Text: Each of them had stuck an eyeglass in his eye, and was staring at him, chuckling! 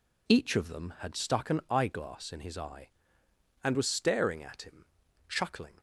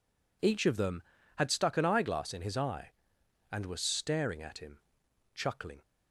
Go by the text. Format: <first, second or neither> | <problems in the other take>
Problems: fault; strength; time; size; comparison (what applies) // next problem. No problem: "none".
neither | none